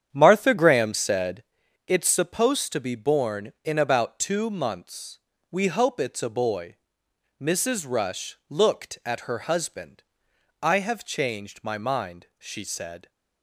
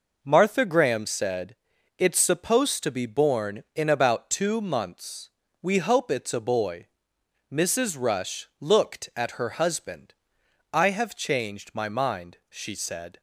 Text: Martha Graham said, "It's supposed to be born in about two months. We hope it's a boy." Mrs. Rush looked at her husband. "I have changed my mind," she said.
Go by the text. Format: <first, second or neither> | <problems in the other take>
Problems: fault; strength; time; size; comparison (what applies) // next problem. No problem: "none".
second | starts louder than the rest; strong; until 1.5 s; 8.5 dB